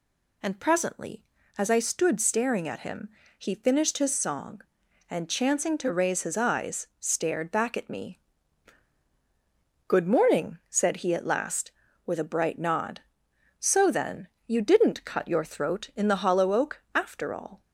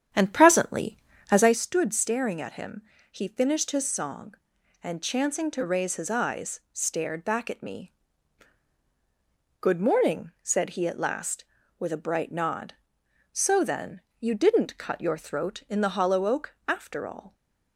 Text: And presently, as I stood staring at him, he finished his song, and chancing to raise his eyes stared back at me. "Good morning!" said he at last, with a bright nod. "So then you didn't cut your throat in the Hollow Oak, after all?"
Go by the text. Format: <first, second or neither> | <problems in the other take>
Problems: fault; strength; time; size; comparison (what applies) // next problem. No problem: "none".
first | starts louder than the rest; strong; until 1.6 s; 9 dB // pauses between "then" and "you"; slight; at 13.9 s; 0.20 s long; slight in the first